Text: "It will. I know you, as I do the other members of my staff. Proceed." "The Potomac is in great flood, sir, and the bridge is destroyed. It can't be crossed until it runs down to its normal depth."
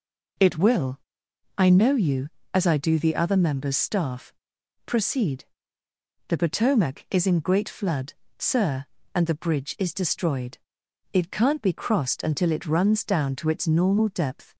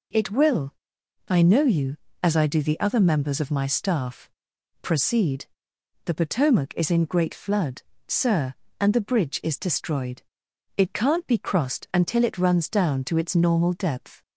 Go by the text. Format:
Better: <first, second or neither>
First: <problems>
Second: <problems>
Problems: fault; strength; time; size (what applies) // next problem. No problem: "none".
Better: second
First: skips "of my"; at 3.7 s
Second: none